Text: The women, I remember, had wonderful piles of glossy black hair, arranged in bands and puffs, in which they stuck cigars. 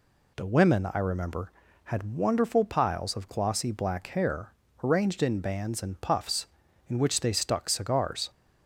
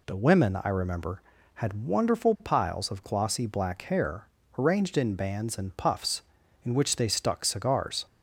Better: neither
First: none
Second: none

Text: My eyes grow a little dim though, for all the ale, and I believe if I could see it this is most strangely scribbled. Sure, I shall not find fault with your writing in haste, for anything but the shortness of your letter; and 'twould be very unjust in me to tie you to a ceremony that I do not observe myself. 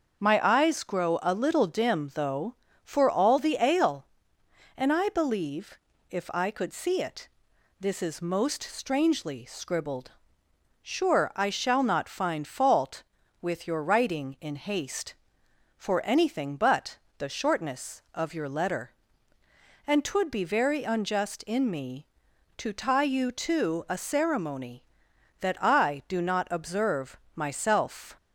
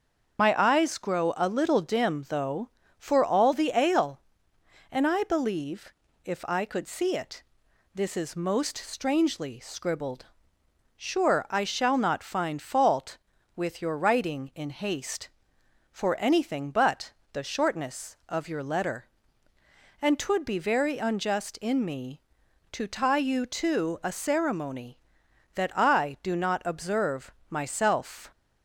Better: first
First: starts louder than the rest; until 1.2 s; 7 dB // pauses between "believe" and "if"; slight; at 5.7 s; 0.32 s long // pauses between "it" and "this"; noticeable; at 7.2 s; 0.52 s long // pauses between "but" and "the"; slight; at 16.9 s; 0.22 s long // pauses between "observe" and "myself"; slight; at 27.1 s; 0.16 s long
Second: loses the start of "My"; at 0.3 s; 45 ms // starts louder than the rest; strong; until 1.4 s; 7 dB // pauses between "believe" and "if"; slight; at 5.9 s; 0.32 s long // pauses between "it" and "this"; noticeable; at 7.4 s; 0.52 s long // pauses between "but" and "the"; slight; at 17.1 s; 0.22 s long // pauses between "observe" and "myself"; slight; at 27.3 s; 0.16 s long

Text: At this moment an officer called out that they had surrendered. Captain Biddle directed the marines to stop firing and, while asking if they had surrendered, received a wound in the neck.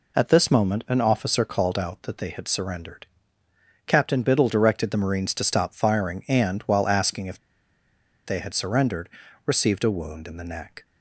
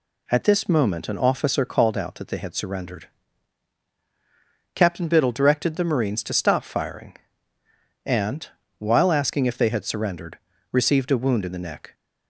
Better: second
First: pauses between "if" and "they"; noticeable; at 7.3 s; 0.87 s long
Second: none

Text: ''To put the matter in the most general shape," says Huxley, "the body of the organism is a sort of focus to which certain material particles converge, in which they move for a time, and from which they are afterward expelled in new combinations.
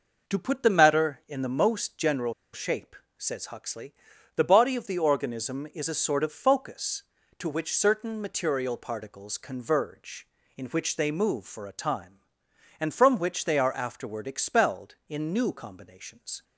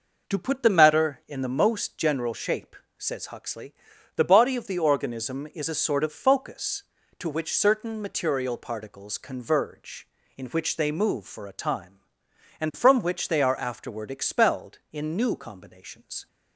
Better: second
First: pauses between "general" and "shape"; slight; at 2.3 s; 0.19 s long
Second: none

